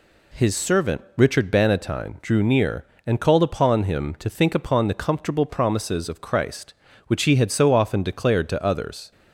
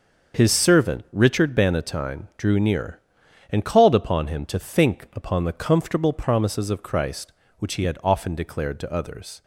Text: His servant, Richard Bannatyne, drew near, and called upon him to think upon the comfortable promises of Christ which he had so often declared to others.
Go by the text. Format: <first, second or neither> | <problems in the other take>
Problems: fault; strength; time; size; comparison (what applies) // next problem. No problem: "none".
first | starts louder than the rest; until 1.4 s; 6.5 dB // skips "so"; at 8.0 s